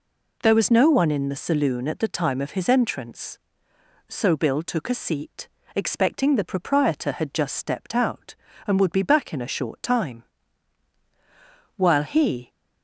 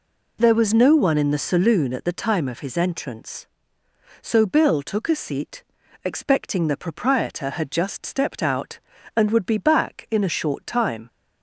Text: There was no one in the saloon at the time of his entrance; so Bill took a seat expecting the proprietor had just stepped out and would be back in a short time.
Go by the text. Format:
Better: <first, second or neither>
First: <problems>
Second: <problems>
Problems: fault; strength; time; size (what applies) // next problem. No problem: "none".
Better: second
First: pauses between "seat" and "expecting"; slight; at 5.4 s; 0.28 s long // goes on to say "While he"; noticeable; from 11.7 s on; 0.76 s long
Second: pauses between "seat" and "expecting"; at 5.6 s; 0.38 s long